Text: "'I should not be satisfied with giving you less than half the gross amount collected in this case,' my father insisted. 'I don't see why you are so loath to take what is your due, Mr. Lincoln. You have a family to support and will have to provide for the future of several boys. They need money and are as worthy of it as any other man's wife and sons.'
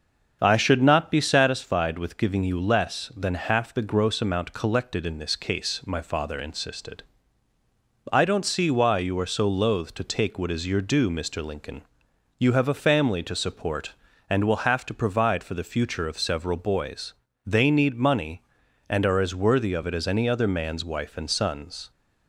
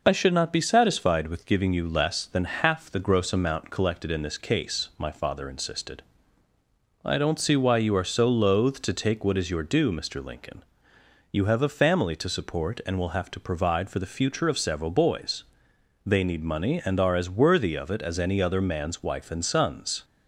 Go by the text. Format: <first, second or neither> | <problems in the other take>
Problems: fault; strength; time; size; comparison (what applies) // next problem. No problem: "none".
second | starts louder than the rest; until 1.5 s; 7 dB